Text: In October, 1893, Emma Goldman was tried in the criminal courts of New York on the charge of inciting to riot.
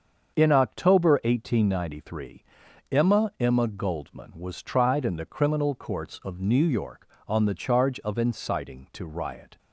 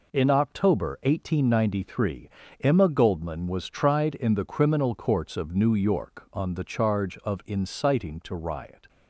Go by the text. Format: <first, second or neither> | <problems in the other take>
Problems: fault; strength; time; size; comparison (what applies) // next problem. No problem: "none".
second | starts louder than the rest; until 1.4 s; 7 dB // says "Emma" twice; at 3.3 s